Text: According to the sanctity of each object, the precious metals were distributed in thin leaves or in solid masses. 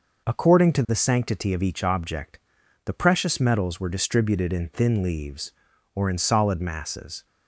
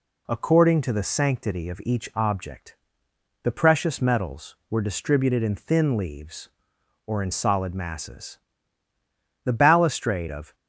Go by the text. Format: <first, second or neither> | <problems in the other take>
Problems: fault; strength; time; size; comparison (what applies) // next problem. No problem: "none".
first | goes on to say "The balustrade of"; noticeable; from 9.4 s on; 1.1 s long